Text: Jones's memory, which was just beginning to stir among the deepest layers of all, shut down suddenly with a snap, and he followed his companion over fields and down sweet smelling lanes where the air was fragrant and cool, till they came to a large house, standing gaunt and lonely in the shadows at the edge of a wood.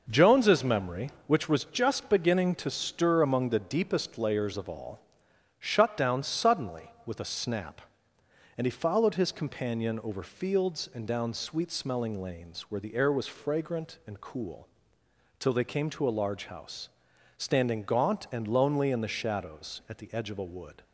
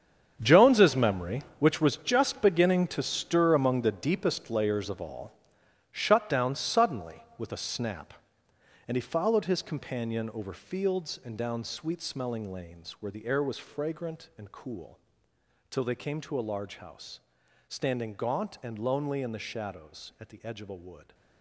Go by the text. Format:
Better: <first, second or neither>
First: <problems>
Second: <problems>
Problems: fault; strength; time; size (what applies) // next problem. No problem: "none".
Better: first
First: none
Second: gets quieter; strong; throughout; 13 dB